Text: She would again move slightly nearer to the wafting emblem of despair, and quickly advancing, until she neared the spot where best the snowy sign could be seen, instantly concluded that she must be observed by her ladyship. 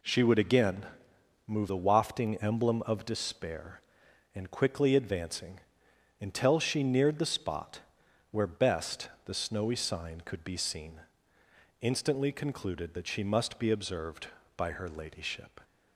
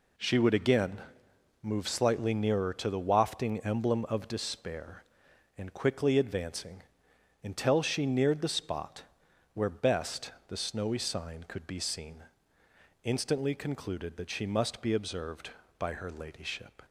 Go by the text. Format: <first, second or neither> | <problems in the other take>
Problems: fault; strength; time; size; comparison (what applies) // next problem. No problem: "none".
second | pauses between "again" and "move"; noticeable; at 0.8 s; 0.62 s long; noticeable in the second // skips "slightly nearer to"; at 1.6 s // pauses between "spot" and "where"; noticeable; at 7.7 s; 0.52 s long; noticeable in the second // pauses between "best" and "the"; slight; at 9.0 s; 0.16 s long; slight in the second